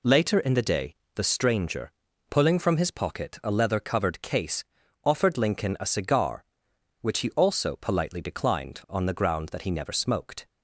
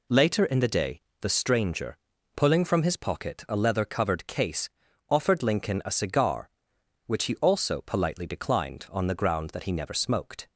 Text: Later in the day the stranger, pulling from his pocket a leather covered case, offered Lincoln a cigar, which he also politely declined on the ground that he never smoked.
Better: neither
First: pauses between "day" and "the"; slight; at 0.9 s; 0.22 s long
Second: pauses between "day" and "the"; slight; at 0.9 s; 0.22 s long

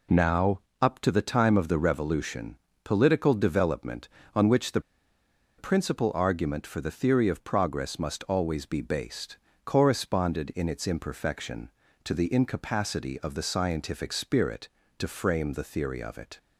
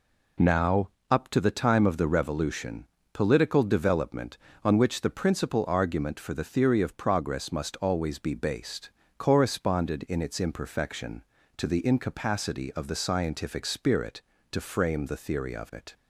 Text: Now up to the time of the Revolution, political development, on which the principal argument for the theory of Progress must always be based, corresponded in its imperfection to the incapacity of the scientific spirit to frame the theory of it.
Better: second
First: pauses between "Now" and "up"; slight; at 0.6 s; 0.20 s long // pauses between "the" and "principal"; noticeable; at 4.7 s; 0.78 s long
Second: pauses between "Now" and "up"; slight; at 0.9 s; 0.20 s long

